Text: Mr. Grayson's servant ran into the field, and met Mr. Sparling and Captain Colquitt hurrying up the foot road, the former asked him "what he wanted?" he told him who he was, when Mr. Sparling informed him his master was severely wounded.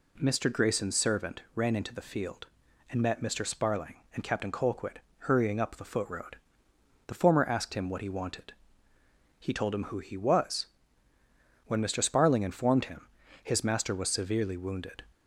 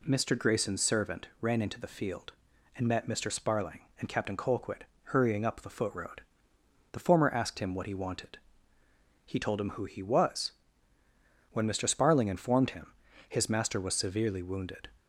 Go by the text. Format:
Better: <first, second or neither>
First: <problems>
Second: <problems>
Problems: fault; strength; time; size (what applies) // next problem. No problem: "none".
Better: neither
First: pauses between "Colquitt" and "hurrying"; slight; at 5.0 s; 0.18 s long // pauses between "him" and "his"; slight; at 13.0 s; 0.36 s long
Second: pauses between "Colquitt" and "hurrying"; slight; at 4.8 s; 0.18 s long // pauses between "him" and "his"; slight; at 12.9 s; 0.36 s long